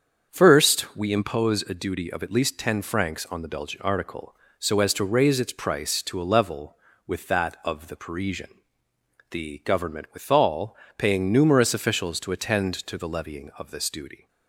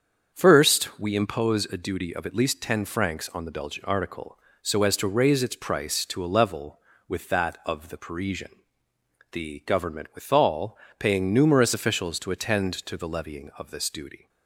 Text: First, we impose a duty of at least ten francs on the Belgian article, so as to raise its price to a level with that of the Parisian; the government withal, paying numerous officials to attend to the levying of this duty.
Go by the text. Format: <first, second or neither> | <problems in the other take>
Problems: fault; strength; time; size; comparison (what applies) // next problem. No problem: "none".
neither | starts louder than the rest; strong; the same in both